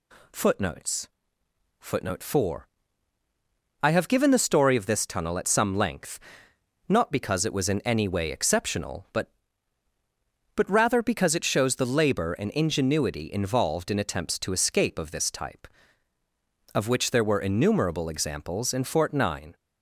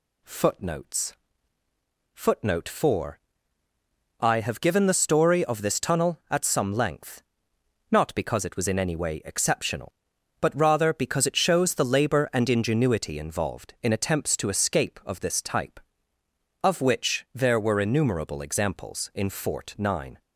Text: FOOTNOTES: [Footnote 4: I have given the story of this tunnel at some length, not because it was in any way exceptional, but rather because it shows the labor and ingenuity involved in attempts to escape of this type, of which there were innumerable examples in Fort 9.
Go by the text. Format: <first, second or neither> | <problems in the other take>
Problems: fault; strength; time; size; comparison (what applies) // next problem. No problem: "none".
second | says "but" twice; at 10.5 s